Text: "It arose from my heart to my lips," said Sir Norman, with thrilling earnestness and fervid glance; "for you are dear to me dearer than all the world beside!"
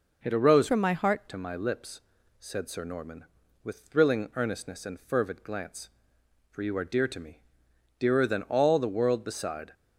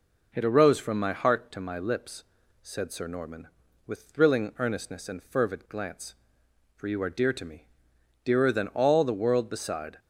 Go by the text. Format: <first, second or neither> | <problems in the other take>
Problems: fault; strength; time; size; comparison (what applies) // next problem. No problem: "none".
second | changes voice from "from" to "heart"; from 0.6 to 1.2 s; 0.6 s long // pauses between "me" and "dearer"; noticeable; at 7.4 s; 0.56 s long; noticeable in the second